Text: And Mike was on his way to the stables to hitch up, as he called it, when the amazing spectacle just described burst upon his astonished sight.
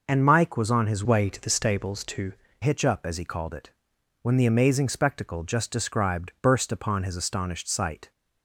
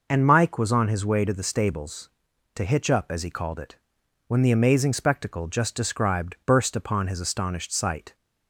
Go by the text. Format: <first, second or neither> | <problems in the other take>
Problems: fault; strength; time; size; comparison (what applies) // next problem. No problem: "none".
second | changes voice from "way" to "to"; from 1.0 to 2.3 s; 1.3 s long